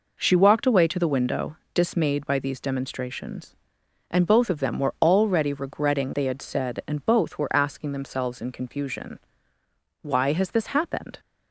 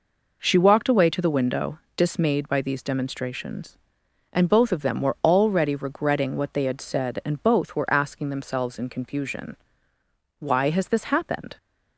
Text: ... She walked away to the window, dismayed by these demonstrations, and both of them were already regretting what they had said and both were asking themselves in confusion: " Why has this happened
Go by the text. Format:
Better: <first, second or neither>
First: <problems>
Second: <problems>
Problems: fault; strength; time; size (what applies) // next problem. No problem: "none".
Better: second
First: skips "what"; at 6.1 s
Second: none